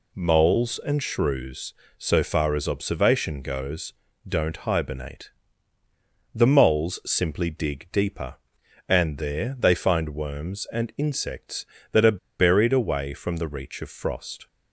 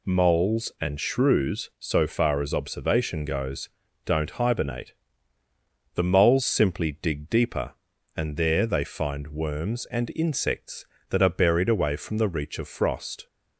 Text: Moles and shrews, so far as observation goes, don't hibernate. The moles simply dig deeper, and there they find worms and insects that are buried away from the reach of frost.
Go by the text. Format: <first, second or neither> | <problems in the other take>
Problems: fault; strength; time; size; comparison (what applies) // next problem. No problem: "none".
second | pauses between "are" and "buried"; slight; at 12.1 s; 0.20 s long